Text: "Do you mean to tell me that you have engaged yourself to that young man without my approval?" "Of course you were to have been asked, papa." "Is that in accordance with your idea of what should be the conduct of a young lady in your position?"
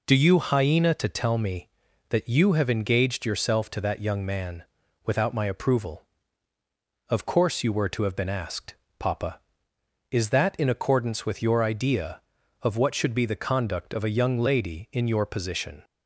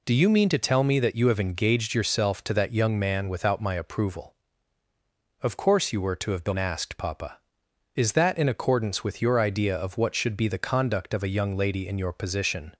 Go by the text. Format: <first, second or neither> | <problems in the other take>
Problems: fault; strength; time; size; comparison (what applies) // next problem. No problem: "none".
second | says "hyena" for "mean"; at 0.3 s // pauses between "man" and "without"; at 4.6 s; 0.42 s long